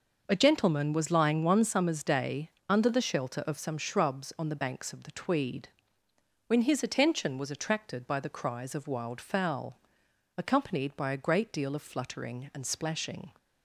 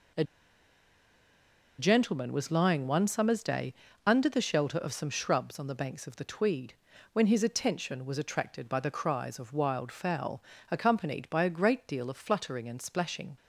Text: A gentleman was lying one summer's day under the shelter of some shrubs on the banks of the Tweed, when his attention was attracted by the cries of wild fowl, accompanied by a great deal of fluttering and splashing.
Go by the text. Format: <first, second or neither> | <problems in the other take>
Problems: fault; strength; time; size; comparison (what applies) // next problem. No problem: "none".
first | pauses between "A" and "gentleman"; strong; at 0.2 s; 1.5 s long // pauses between "day" and "under"; slight; at 3.7 s; 0.32 s long; slight in the first